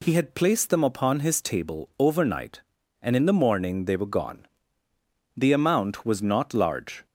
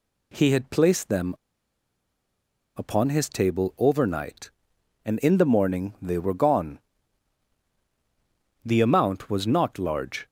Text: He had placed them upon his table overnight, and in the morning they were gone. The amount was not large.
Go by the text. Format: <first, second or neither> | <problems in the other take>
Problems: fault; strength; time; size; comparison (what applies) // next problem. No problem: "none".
first | pauses between "them" and "upon"; strong; at 1.3 s; 1.4 s long